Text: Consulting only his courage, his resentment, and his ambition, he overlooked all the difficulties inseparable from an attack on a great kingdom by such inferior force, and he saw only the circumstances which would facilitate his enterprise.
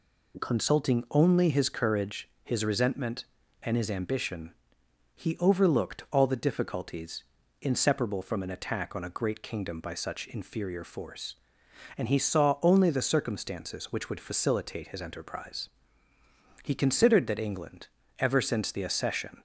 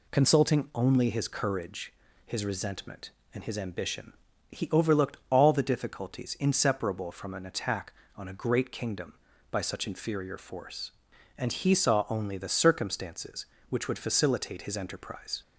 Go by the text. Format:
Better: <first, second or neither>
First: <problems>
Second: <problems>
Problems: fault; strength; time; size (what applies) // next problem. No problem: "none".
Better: second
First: pauses between "difficulties" and "inseparable"; at 7.2 s; 0.38 s long // goes on to say "He considered that England ever since the accession"; strong; from 16.6 s on; 2.8 s long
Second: none